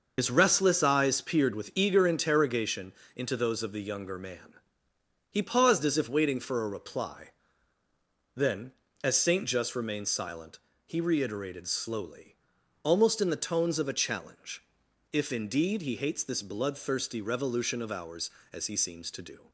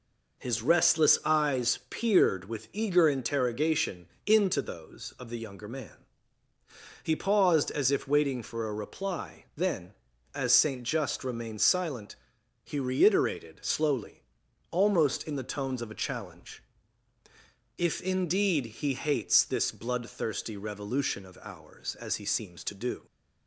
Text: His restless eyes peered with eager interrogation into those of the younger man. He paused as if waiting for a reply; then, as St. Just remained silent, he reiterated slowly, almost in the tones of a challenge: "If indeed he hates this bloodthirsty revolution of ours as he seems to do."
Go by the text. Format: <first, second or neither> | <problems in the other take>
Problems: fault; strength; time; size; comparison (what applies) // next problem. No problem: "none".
second | loses the start of "His"; at 0.1 s; 65 ms // starts louder than the rest; noticeable; until 1.1 s; 6 dB // pauses between "interrogation" and "into"; slight; at 2.9 s; 0.24 s long; slight in the second